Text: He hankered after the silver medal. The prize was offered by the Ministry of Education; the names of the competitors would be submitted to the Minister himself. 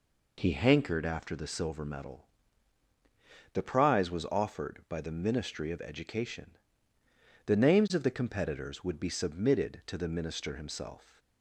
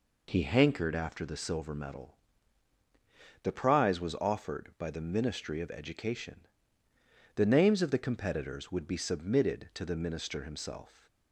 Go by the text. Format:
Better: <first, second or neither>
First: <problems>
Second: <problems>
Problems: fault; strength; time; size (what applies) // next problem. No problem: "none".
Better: neither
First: none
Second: none